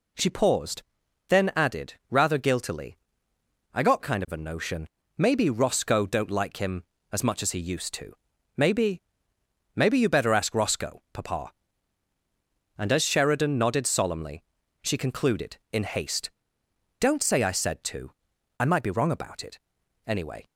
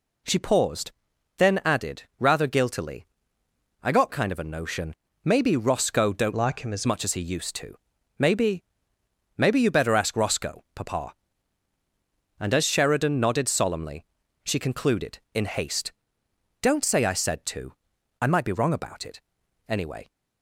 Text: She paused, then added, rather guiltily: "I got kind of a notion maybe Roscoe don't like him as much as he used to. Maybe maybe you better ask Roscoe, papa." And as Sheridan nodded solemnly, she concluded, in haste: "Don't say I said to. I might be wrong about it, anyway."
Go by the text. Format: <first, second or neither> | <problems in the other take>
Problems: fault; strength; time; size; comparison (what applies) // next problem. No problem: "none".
first | pauses between "notion" and "maybe"; slight; at 4.9 s; 0.30 s long; slight in the first // changes voice from "like" to "as"; from 6.3 to 6.8 s; 0.5 s long // pauses between "Maybe" and "maybe"; noticeable; at 8.6 s; 0.74 s long; noticeable in the first